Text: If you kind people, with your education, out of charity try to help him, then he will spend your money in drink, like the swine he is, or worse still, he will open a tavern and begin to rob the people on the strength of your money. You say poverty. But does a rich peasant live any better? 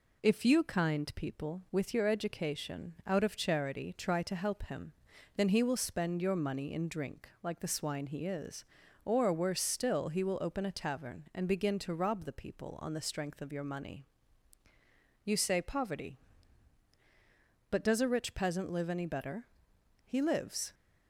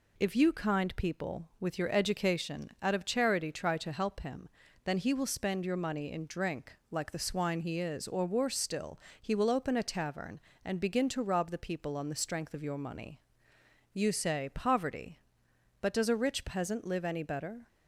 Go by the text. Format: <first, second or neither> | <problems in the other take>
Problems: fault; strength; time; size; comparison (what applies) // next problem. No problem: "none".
second | goes on to say "He lives"; noticeable; from 20.0 s on; 0.70 s long